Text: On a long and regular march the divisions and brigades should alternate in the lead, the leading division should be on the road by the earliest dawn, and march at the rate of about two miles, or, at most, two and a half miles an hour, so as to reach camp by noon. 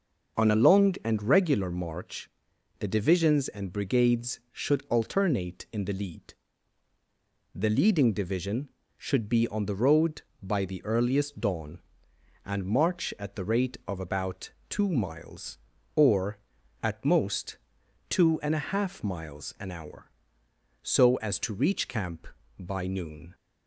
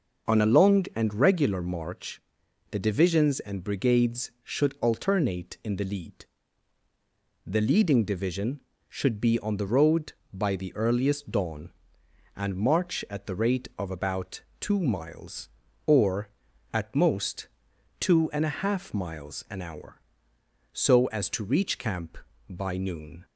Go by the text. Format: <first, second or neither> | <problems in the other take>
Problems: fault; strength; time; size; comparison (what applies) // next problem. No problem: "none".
neither | starts louder than the rest; the same in both // pauses between "march" and "the"; noticeable; the same in both // pauses between "about" and "two"; slight; the same in both